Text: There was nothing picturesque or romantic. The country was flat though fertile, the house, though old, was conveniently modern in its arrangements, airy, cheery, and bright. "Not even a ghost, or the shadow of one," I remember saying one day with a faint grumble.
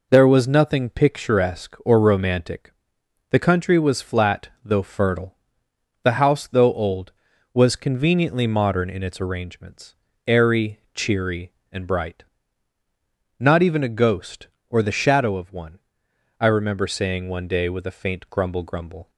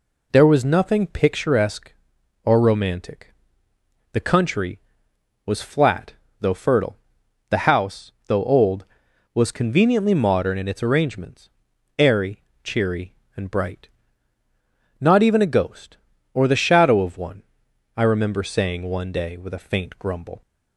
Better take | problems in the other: second | pauses between "flat" and "though"; slight; at 4.4 s; 0.16 s long; slight in the second // says "grumble" twice; at 18.6 s

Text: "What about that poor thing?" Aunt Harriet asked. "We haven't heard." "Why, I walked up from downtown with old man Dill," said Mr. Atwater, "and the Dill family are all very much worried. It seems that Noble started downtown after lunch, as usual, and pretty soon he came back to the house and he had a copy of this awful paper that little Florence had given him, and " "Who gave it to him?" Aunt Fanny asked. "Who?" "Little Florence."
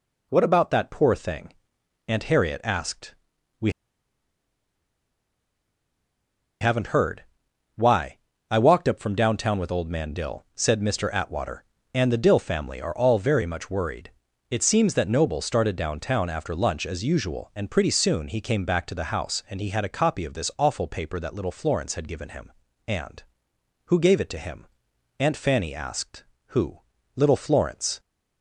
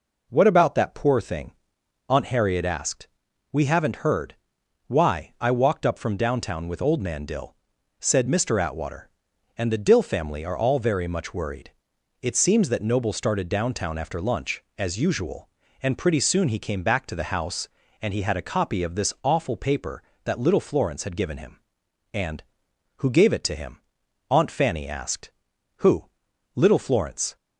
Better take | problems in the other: second | pauses between "We" and "haven't"; strong; at 3.7 s; 2.8 s long

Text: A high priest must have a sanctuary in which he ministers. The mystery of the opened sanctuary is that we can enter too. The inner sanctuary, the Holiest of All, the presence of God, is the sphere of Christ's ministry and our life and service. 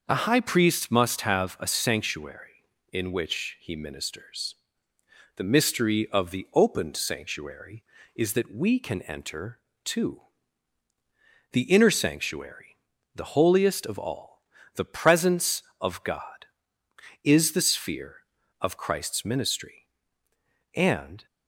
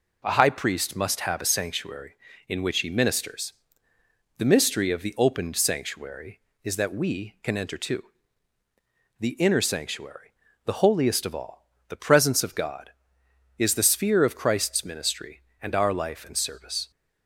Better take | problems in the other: second | starts louder than the rest; noticeable; until 1.0 s; 6 dB // pauses between "enter" and "too"; slight; at 9.5 s; 0.26 s long // stops before "our life and service"; at 21.2 s

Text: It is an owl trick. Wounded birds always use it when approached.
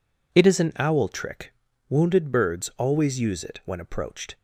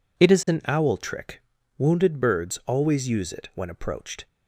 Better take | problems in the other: neither | none

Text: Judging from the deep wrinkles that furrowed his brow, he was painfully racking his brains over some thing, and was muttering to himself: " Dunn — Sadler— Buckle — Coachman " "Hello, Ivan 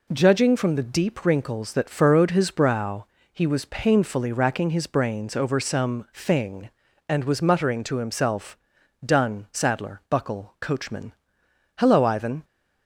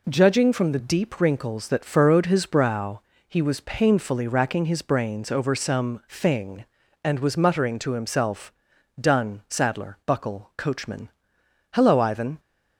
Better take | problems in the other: neither | none

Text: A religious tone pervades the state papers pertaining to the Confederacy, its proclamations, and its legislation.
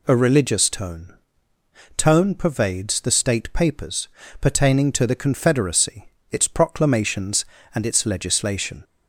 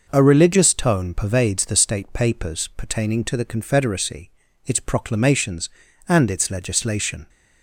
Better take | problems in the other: second | says "tone" twice; at 1.9 s // pauses between "papers" and "pertaining"; slight; at 4.0 s; 0.32 s long

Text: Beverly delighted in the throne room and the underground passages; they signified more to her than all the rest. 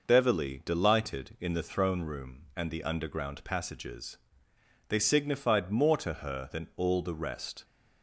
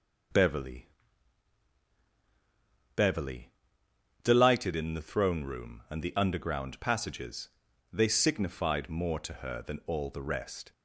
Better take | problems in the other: first | says "Beverly" twice; at 2.9 s

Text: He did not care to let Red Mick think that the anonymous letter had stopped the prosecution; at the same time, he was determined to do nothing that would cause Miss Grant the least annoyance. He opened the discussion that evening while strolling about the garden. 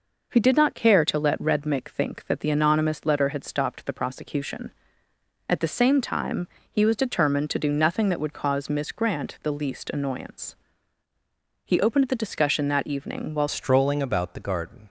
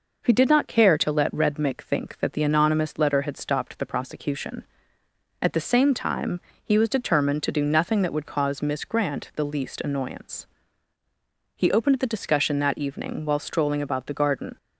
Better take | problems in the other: second | changes voice at "strolling"; from 13.4 s on; 1.4 s long

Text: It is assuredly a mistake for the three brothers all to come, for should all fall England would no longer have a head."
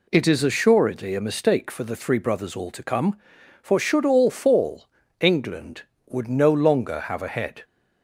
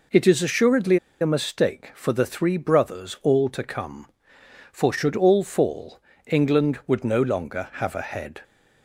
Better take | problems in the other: first | pauses between "assuredly" and "a"; slight; at 0.9 s; 0.24 s long // pauses between "fall" and "England"; slight; at 5.9 s; 0.26 s long; slight in the first

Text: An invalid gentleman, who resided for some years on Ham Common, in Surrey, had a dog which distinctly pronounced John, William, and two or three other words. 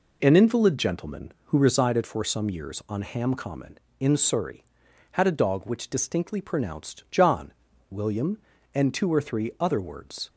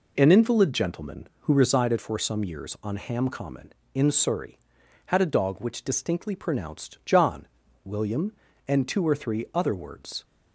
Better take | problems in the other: neither | none

